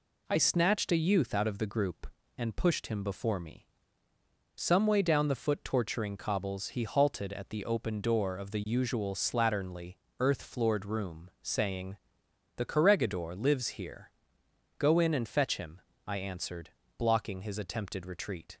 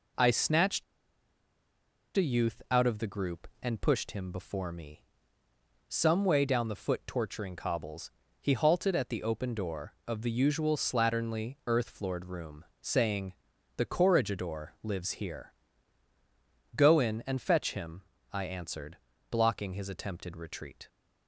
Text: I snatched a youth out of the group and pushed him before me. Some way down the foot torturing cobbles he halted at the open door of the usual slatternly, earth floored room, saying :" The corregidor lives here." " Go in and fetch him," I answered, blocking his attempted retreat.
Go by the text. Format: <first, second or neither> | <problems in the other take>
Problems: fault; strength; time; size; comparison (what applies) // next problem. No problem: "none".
first | pauses between "snatched" and "a"; strong; at 0.8 s; 1.3 s long // pauses between "cobbles" and "he"; slight; at 8.0 s; 0.32 s long